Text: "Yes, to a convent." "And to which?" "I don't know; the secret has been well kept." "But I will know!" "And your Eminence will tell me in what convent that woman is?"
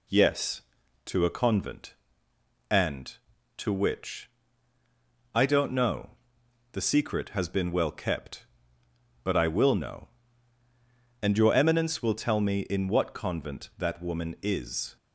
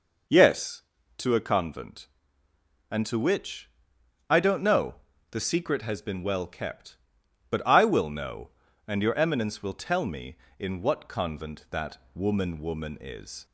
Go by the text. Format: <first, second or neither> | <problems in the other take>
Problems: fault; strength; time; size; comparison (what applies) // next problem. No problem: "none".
first | pauses between "that" and "woman"; slight; at 11.9 s; 0.16 s long // says "woman" twice; at 12.5 s